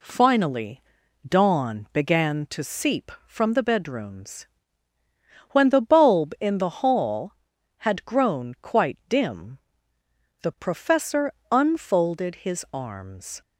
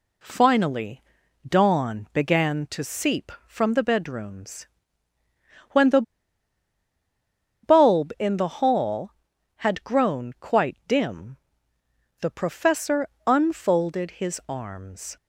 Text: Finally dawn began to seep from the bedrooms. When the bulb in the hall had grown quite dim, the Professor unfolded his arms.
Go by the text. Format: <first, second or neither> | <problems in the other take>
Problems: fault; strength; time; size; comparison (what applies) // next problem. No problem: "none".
first | pauses between "Finally" and "dawn"; at 1.0 s; 0.44 s long; also in the first // pauses between "the" and "bulb"; strong; at 6.0 s; 1.6 s long // pauses between "Professor" and "unfolded"; slight; at 13.0 s; 0.20 s long; slight in the first